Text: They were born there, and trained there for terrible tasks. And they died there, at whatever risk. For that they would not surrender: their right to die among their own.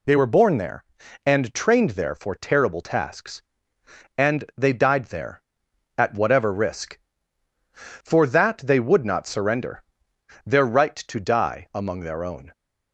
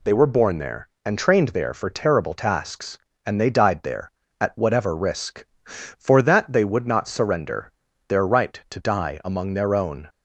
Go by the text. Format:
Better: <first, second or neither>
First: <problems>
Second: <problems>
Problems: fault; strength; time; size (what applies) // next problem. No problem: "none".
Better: neither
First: none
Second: none